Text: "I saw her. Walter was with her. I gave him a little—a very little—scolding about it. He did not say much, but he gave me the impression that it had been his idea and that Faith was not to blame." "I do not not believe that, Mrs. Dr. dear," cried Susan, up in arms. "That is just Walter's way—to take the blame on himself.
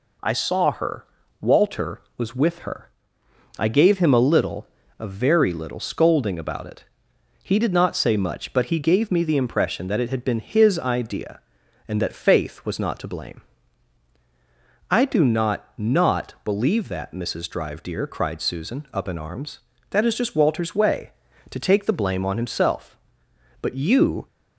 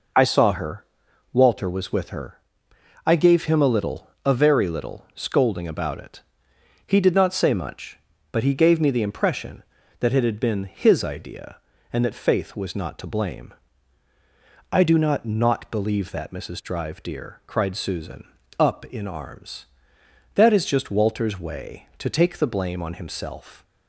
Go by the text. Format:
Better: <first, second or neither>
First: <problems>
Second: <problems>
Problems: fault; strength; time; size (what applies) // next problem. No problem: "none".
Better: second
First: goes on to say "But you"; noticeable; from 23.6 s on; 0.66 s long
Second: none